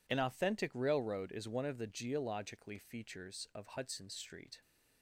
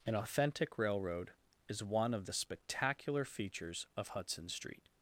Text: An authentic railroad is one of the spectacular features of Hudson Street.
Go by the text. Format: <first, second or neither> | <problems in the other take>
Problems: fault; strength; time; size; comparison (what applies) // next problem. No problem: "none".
second | says "geologically" for "spectacular"; at 1.8 s